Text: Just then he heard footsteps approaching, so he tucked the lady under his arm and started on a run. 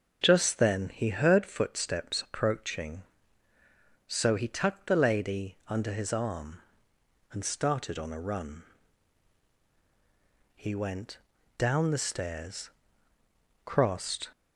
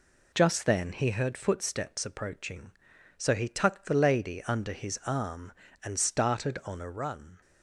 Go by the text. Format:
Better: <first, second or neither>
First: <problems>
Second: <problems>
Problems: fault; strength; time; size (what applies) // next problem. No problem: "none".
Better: second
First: starts louder than the rest; until 1.2 s; 7 dB // goes on to say "He went down the stairs crossed"; strong; from 10.5 s on; 3.7 s long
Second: none